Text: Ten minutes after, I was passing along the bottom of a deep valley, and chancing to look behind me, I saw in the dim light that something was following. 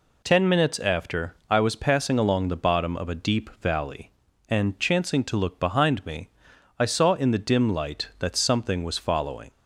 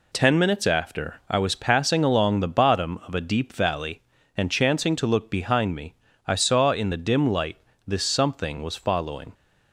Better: first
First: none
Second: says "this" for "that"; at 7.8 s

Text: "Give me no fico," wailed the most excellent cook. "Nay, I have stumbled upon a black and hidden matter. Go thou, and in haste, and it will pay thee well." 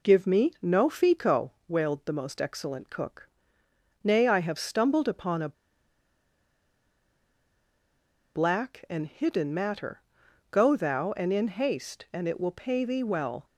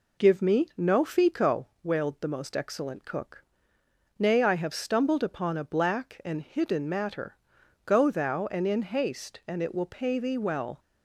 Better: second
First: pauses between "a" and "black"; strong; at 5.5 s; 2.8 s long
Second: none

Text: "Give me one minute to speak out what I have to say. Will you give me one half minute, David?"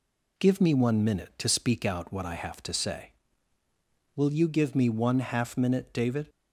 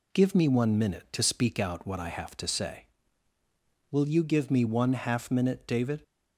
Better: neither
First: none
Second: none

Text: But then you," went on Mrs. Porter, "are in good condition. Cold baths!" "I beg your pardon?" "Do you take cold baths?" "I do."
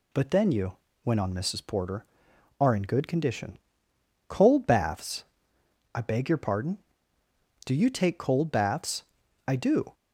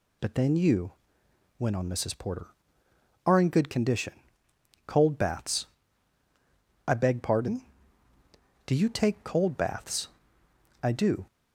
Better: first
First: none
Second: skips "your"; at 7.2 s

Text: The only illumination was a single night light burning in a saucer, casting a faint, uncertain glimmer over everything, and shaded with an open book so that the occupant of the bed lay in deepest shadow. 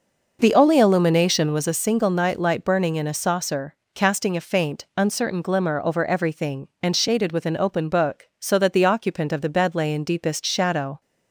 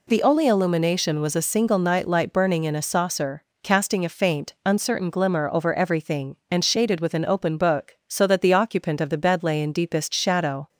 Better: second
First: starts louder than the rest; noticeable; until 1.7 s; 5.5 dB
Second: none

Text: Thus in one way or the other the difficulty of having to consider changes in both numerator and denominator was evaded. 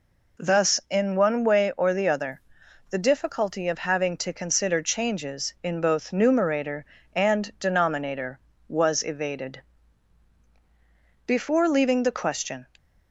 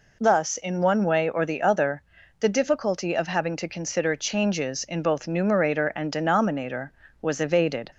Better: second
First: pauses between "other" and "the"; noticeable; at 2.4 s; 0.50 s long // goes on to say "Before leaving the question"; from 11.2 s on; 1.4 s long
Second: pauses between "other" and "the"; at 2.0 s; 0.38 s long

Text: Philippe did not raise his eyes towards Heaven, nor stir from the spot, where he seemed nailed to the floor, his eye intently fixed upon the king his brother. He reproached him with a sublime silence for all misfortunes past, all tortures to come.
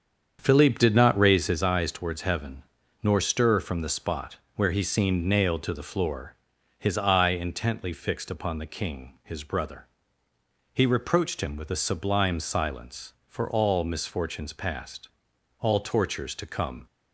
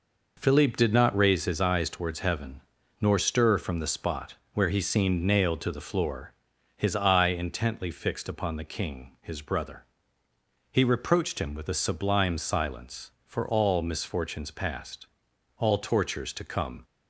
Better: second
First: starts louder than the rest; strong; until 1.7 s; 7.5 dB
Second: none

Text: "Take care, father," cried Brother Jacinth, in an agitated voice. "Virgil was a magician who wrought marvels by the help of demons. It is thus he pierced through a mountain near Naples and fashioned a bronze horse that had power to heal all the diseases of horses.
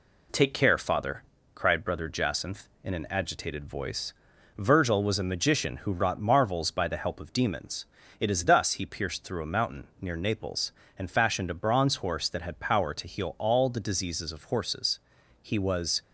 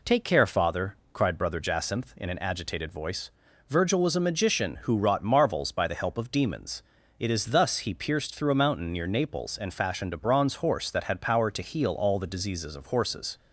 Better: second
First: goes on to say "He was"; from 15.4 s on; 0.60 s long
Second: none

